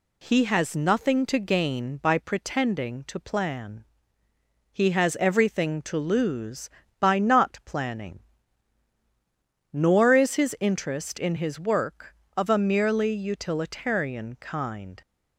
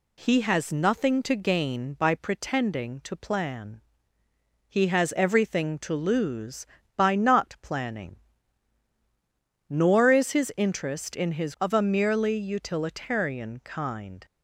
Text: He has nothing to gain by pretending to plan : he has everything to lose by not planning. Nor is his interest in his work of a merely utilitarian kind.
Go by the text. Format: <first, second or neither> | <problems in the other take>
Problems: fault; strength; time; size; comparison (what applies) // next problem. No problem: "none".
first | skips "work"; at 11.5 s